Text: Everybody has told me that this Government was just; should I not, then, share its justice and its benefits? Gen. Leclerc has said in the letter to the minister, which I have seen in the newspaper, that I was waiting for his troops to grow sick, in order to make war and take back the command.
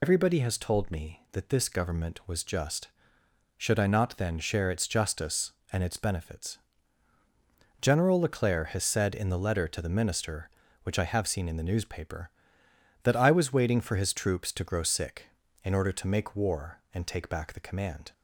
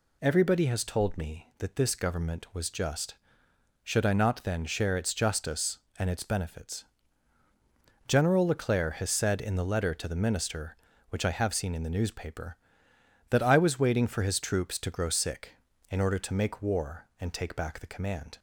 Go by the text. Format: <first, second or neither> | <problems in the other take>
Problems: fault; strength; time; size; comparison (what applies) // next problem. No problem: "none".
second | loses the start of "Everybody"; at 0.0 s; 80 ms